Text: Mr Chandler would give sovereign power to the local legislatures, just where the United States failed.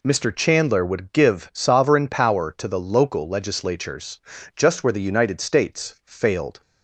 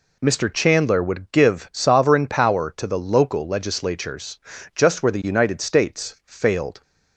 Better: neither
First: none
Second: none

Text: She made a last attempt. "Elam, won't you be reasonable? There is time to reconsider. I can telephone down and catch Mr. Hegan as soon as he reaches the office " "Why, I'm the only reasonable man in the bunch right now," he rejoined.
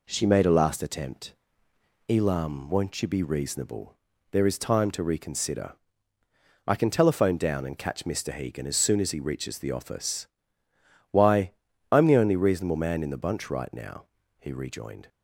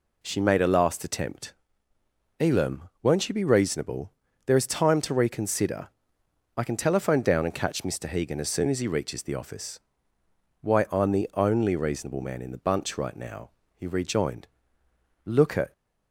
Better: first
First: none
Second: goes on to say "Look at"; slight; from 15.2 s on; 0.48 s long

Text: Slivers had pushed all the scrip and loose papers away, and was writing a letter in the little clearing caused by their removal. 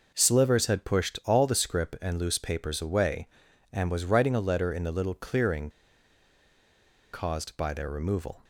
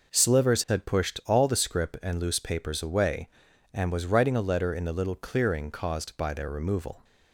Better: second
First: pauses between "clearing" and "caused"; strong; at 5.7 s; 1.4 s long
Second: none

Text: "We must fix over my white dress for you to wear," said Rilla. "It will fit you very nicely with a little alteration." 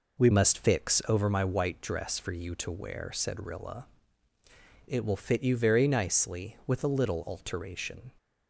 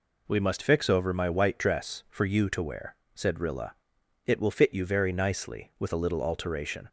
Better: second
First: changes voice at "must"; from 0.3 s on; 7.8 s long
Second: none

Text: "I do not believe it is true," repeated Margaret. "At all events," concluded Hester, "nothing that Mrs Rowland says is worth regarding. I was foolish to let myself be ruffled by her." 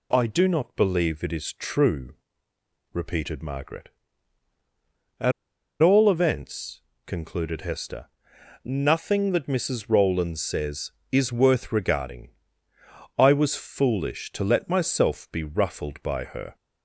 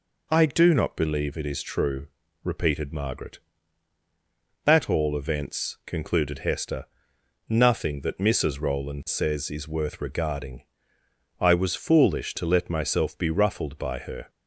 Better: second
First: pauses between "At" and "all"; noticeable; at 5.3 s; 0.49 s long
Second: none

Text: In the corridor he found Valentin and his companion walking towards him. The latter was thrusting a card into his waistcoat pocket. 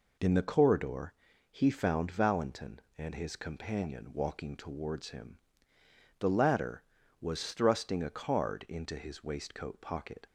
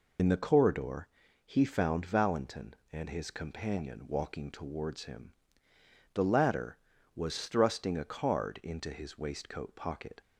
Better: first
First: pauses between "corridor" and "he"; at 1.1 s; 0.38 s long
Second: loses the start of "In"; at 0.1 s; 55 ms // pauses between "corridor" and "he"; at 1.0 s; 0.38 s long

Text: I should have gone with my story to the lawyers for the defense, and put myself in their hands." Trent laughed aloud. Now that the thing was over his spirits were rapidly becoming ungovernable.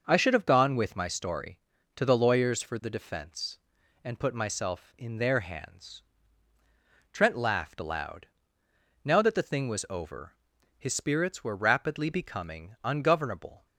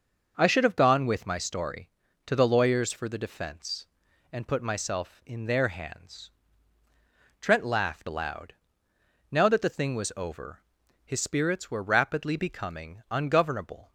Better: neither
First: pauses between "over" and "his"; noticeable; at 10.3 s; 0.46 s long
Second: pauses between "over" and "his"; noticeable; at 10.5 s; 0.46 s long

